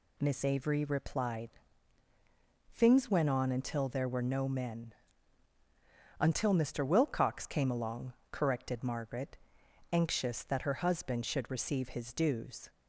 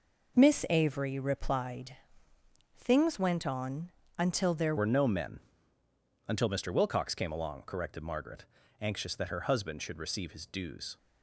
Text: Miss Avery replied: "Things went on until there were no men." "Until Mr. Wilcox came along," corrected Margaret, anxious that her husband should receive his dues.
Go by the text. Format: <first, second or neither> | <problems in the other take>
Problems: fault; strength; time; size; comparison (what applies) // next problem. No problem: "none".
first | pauses between "on" and "until"; slight; at 3.9 s; 0.26 s long // changes voice at "were"; from 4.7 s on; 6.2 s long